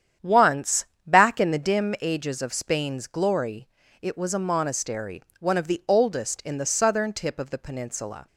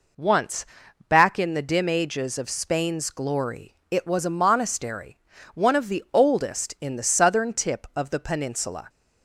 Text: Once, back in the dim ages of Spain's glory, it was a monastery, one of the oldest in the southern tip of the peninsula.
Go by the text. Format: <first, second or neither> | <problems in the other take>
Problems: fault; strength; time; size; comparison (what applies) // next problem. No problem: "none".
second | starts louder than the rest; strong; until 1.8 s; 9 dB